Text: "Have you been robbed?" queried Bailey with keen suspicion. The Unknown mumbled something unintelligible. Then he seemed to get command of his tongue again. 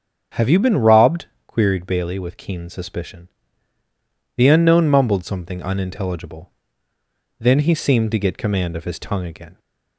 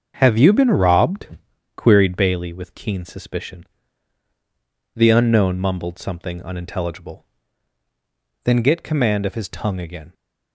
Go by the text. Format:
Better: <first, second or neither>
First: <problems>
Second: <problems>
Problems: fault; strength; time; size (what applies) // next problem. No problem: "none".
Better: first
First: starts louder than the rest; strong; until 1.5 s; 7.5 dB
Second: starts louder than the rest; until 1.2 s; 7 dB // skips "he seemed to"; at 8.6 s